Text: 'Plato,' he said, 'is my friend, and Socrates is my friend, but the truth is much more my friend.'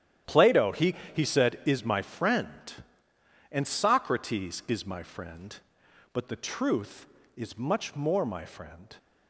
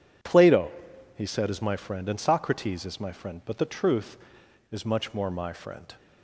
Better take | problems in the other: second | starts louder than the rest; strong; until 1.4 s; 11 dB // says "he" twice; at 1.1 s

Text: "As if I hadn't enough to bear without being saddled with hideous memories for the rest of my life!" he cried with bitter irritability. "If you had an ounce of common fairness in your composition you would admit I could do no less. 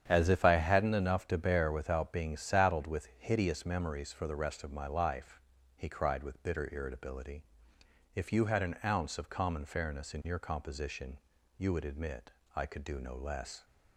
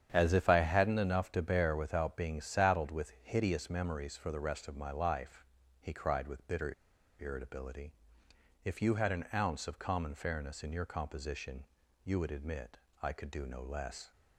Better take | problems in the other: first | starts louder than the rest; strong; until 1.1 s; 9 dB; strong in the first // pauses between "bitter" and "irritability"; noticeable; at 6.7 s; 0.47 s long // pauses between "composition" and "you"; at 11.6 s; 0.40 s long; also in the first // pauses between "admit" and "I"; slight; at 12.7 s; 0.24 s long; slight in the first

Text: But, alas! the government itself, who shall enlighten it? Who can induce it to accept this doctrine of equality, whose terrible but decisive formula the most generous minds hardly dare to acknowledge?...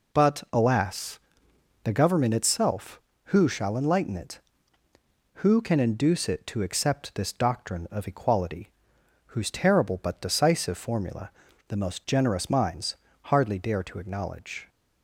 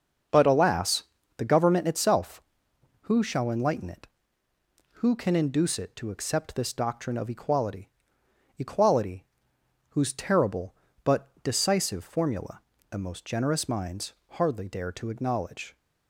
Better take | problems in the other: first | starts louder than the rest; until 1.6 s; 6.5 dB // says "equality" twice; at 8.5 s // pauses between "formula" and "the"; slight; at 12.5 s; 0.30 s long; also in the first // pauses between "minds" and "hardly"; slight; at 14.1 s; 0.18 s long; slight in the first

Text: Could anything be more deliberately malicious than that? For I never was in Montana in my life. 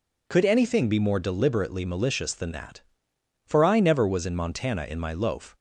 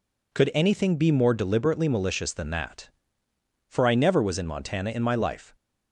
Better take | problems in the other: second | says "loaf" for "life"; at 5.1 s

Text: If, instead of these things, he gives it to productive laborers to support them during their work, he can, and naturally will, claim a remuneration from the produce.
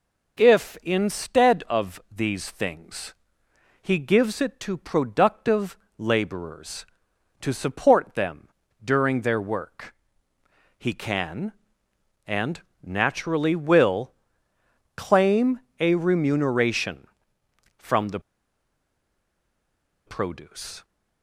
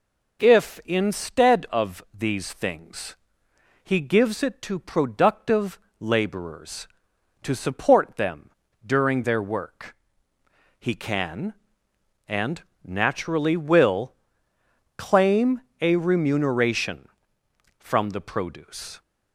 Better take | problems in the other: second | pauses between "productive" and "laborers"; slight; at 5.7 s; 0.22 s long; slight in the second // pauses between "them" and "during"; slight; at 8.4 s; 0.34 s long; slight in the second // pauses between "and" and "naturally"; slight; at 12.5 s; 0.24 s long; slight in the second // pauses between "claim" and "a"; slight; at 15.5 s; 0.22 s long; slight in the second // pauses between "the" and "produce"; strong; at 18.1 s; 1.8 s long

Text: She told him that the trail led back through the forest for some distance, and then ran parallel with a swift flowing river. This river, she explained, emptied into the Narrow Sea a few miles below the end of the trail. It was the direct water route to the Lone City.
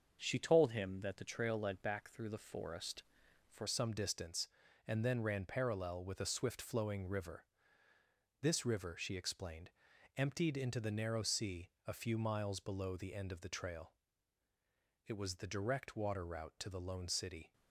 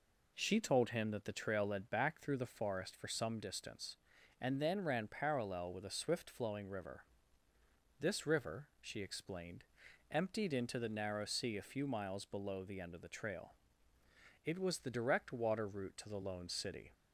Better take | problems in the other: second | starts louder than the rest; until 1.2 s; 6.5 dB // changes voice at "some"; from 3.6 s on; 13.9 s long // pauses between "Sea" and "a"; slight; at 11.6 s; 0.18 s long

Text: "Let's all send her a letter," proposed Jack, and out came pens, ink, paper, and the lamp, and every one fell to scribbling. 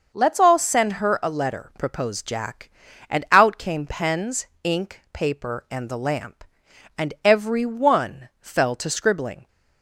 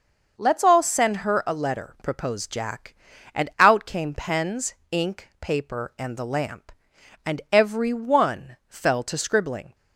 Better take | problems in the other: neither | starts louder than the rest; the same in both

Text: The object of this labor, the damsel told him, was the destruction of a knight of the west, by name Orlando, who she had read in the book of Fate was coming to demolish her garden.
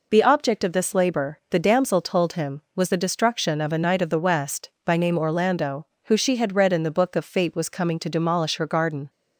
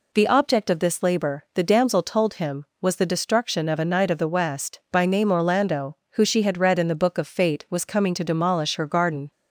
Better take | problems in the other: neither | none

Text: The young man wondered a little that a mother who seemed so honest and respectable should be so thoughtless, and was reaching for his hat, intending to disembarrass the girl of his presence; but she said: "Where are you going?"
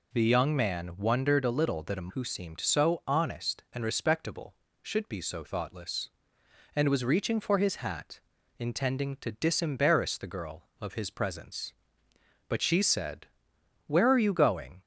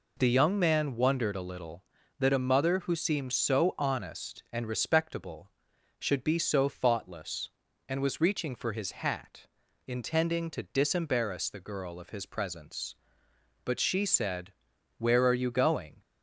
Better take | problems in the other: second | skips "mother"; at 2.1 s

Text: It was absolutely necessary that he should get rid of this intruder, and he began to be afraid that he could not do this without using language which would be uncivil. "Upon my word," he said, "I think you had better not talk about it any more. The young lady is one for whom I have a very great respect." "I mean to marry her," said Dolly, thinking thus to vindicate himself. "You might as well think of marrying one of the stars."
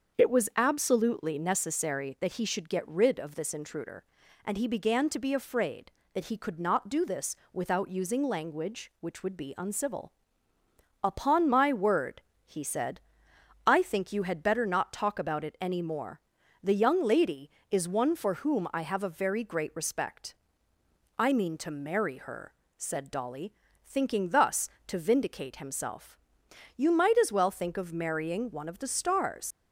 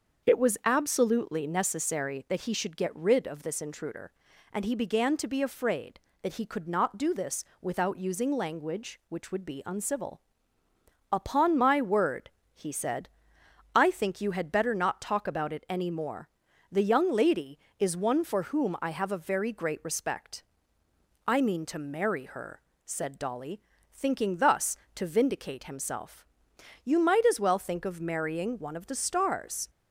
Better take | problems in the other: second | starts louder than the rest; until 1.2 s; 6.5 dB; also in the second // pauses between "this" and "without"; slight; at 7.3 s; 0.16 s long; slight in the second // leaves "stars" unfinished; at 29.5 s; 110 ms

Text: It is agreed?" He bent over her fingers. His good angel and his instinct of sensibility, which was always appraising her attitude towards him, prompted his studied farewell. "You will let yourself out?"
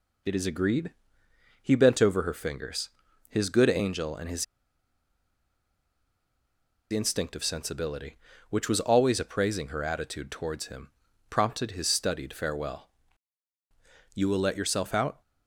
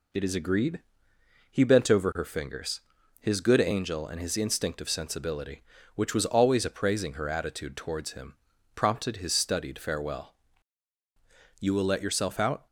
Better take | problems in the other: second | pauses between "his" and "instinct"; strong; at 4.4 s; 2.4 s long

